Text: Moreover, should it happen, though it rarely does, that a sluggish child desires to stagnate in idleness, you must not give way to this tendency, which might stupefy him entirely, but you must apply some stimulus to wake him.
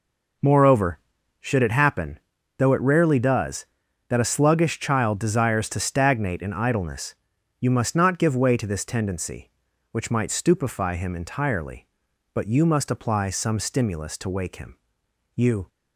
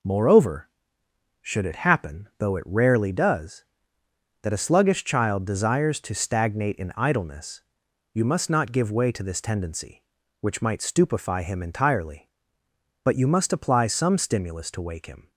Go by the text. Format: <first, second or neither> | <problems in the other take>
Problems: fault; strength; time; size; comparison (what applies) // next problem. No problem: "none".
second | goes on to say "You"; slight; from 15.3 s on; 0.34 s long